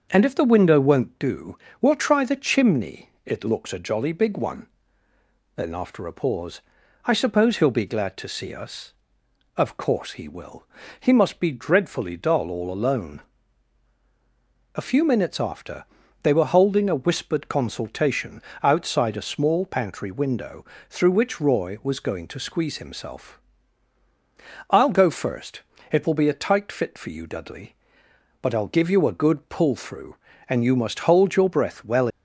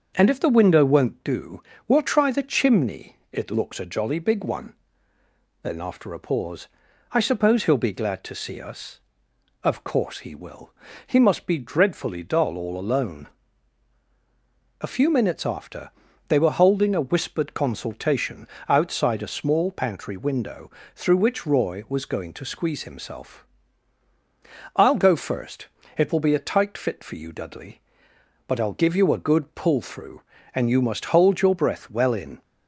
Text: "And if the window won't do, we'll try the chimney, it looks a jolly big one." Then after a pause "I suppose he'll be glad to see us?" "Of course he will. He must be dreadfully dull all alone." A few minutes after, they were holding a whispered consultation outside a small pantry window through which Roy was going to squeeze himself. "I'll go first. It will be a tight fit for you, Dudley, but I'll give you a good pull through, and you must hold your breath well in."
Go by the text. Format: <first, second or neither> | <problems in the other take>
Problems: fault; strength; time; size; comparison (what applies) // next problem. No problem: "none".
second | starts louder than the rest; until 1.1 s; 6.5 dB; also in the second // pauses between "pause" and "I"; at 6.6 s; 0.44 s long; also in the second // pauses between "consultation" and "outside"; slight; at 18.4 s; 0.20 s long; slight in the second // pauses between "window" and "through"; slight; at 20.6 s; 0.26 s long; slight in the second // stops before "in"; at 32.0 s